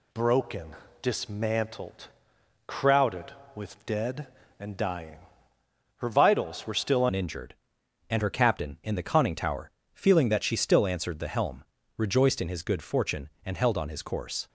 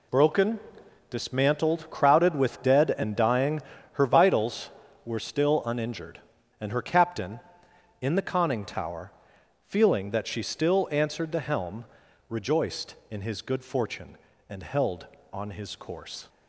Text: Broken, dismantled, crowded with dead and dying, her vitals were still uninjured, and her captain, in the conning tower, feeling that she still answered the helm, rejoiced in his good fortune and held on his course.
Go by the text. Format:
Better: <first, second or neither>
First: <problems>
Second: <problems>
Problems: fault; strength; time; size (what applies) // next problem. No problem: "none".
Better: second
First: changes voice at "uninjured"; from 7.0 s on; 7.4 s long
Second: none